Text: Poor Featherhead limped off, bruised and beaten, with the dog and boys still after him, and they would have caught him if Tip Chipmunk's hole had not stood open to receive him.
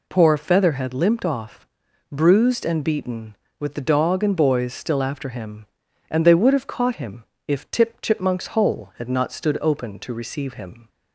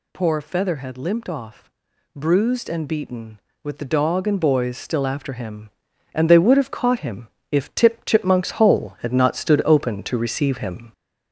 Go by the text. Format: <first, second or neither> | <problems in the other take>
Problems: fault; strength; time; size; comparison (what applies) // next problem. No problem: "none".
first | gets louder; noticeable; throughout; 4 dB // pauses between "him" and "if"; slight; at 7.2 s; 0.22 s long; slight in the first